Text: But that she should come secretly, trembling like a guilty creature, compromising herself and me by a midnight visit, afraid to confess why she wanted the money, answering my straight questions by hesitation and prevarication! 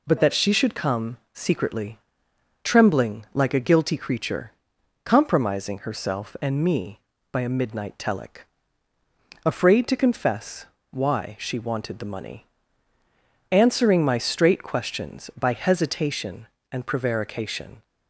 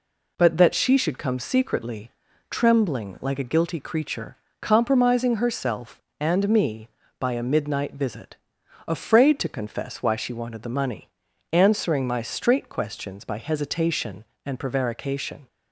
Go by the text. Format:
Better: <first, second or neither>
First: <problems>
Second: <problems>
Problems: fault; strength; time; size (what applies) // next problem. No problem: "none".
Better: second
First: pauses between "come" and "secretly"; slight; at 1.1 s; 0.16 s long // says "telic" for "visit"; at 7.9 s // pauses between "confess" and "why"; slight; at 10.6 s; 0.26 s long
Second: none